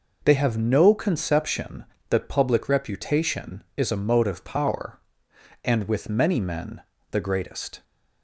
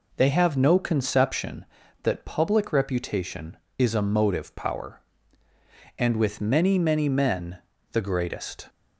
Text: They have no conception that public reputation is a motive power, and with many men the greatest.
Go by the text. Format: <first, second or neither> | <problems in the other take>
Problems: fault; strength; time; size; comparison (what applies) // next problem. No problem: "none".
first | says "many" twice; at 6.7 s // pauses between "men" and "the"; slight; at 7.5 s; 0.34 s long; slight in the first